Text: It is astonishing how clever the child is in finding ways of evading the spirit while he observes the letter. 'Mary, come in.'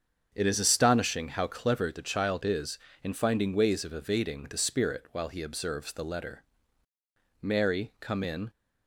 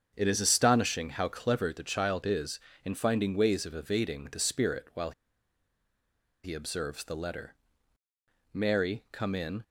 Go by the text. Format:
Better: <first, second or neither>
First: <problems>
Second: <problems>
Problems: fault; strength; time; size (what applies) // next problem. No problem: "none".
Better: first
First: starts louder than the rest; until 1.3 s; 7 dB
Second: starts louder than the rest; until 1.1 s; 7 dB // pauses between "while" and "he"; strong; at 5.1 s; 1.3 s long